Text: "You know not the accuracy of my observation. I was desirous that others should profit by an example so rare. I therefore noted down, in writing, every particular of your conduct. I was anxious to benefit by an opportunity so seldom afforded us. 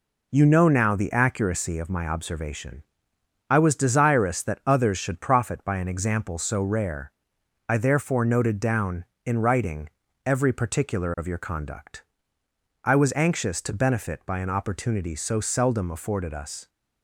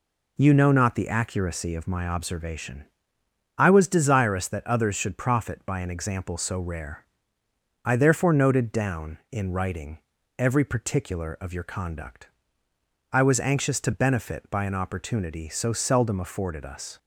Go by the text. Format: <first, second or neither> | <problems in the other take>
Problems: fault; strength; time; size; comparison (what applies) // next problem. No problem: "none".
second | says "now" for "not"; at 0.6 s